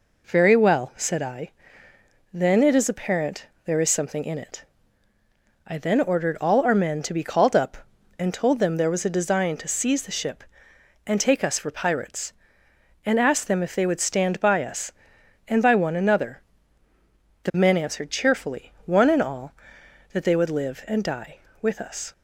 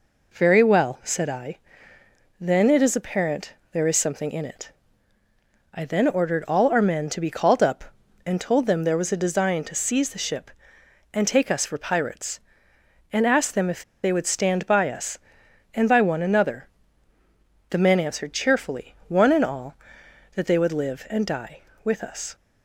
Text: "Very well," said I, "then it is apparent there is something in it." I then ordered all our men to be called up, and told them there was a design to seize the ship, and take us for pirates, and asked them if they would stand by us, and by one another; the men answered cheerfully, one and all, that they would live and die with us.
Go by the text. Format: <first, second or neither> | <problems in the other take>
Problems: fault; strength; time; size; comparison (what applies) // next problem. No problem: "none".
first | pauses between "apparent" and "there"; slight; at 3.5 s; 0.22 s long; slight in the first // pauses between "if" and "they"; slight; at 13.8 s; 0.22 s long